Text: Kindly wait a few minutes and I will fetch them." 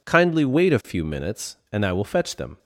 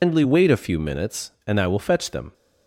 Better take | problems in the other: first | loses the start of "Kindly"; at 0.0 s; 170 ms

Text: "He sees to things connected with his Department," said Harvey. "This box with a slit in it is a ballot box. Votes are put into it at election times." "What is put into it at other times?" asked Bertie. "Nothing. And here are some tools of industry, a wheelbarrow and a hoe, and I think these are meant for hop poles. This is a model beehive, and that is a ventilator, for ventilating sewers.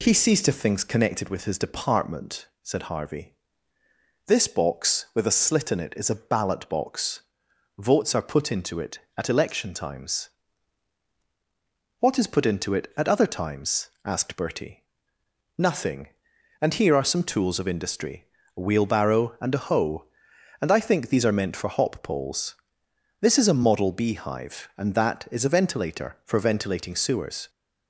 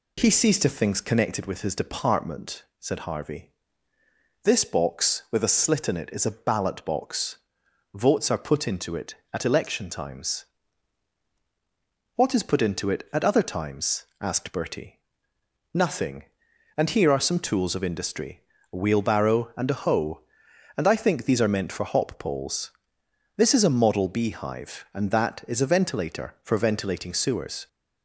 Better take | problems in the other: neither | none

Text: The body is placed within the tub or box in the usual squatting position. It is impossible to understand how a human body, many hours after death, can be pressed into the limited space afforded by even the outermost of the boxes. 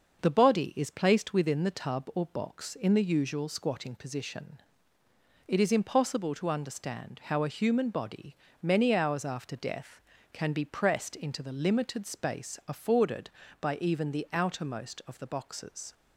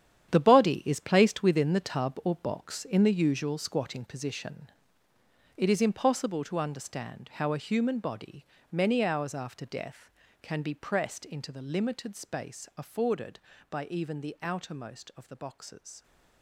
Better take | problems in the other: first | gets quieter; strong; throughout; 12 dB // starts louder than the rest; strong; until 1.3 s; 9.5 dB; also in the first

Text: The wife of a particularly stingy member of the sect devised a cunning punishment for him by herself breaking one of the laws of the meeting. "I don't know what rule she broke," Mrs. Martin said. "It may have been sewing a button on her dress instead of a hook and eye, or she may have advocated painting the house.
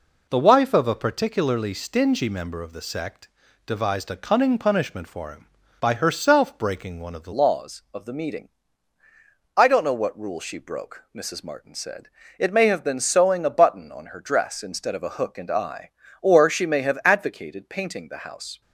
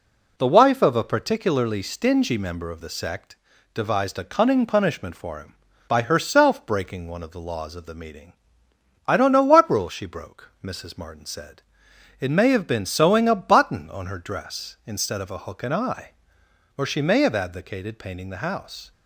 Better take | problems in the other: second | pauses between "sect" and "devised"; slight; at 3.2 s; 0.36 s long; slight in the second // changes voice at "laws"; from 7.3 s on; 11.3 s long

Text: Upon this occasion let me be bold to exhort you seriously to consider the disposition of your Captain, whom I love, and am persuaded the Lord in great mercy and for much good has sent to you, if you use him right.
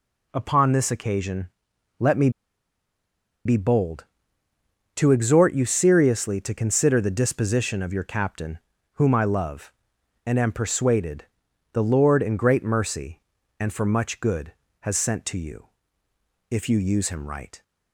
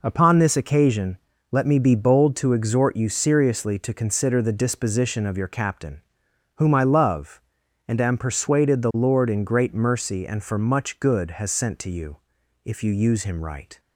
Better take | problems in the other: second | pauses between "occasion" and "let"; noticeable; at 1.4 s; 0.54 s long; slight in the second // pauses between "me" and "be"; at 2.2 s; 1.1 s long // pauses between "persuaded" and "the"; noticeable; at 11.2 s; 0.48 s long

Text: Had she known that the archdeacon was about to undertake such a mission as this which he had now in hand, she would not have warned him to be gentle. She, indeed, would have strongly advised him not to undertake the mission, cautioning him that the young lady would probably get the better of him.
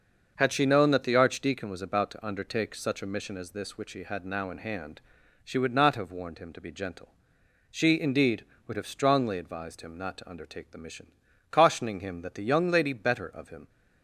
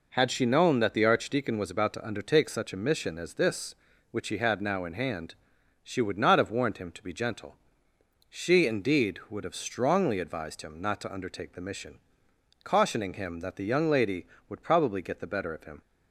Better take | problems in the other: second | starts louder than the rest; until 1.3 s; 6.5 dB // skips "would probably get the"; at 12.9 s

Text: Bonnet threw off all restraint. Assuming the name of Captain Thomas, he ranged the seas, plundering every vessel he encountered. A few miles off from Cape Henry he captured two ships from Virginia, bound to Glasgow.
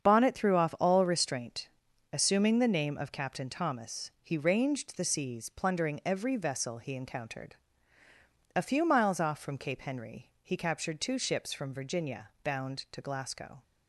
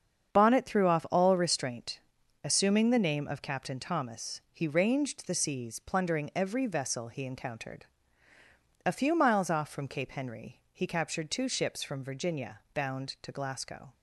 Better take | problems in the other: neither | starts louder than the rest; strong; the same in both

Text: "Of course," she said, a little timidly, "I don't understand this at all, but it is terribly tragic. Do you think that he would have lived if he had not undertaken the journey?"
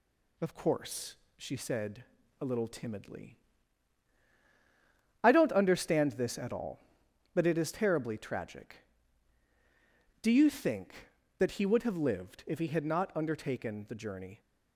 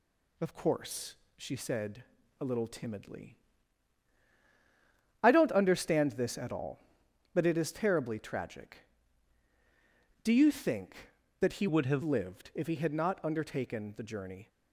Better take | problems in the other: first | changes voice from "would" to "have"; from 11.6 to 12.0 s; 0.4 s long

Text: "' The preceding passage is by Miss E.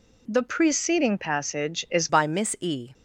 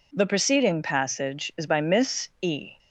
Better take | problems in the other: second | changes voice at "by"; from 2.0 s on; 0.9 s long

